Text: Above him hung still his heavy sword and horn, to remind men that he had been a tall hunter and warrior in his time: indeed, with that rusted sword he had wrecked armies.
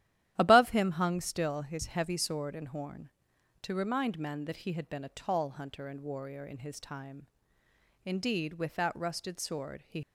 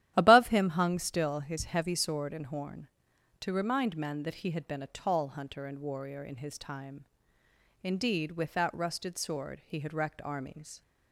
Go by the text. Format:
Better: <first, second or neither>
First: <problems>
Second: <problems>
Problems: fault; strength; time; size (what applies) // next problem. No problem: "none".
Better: second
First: starts louder than the rest; strong; until 1.3 s; 12 dB // stops before "had wrecked armies"; at 10.0 s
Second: starts louder than the rest; strong; until 1.1 s; 12 dB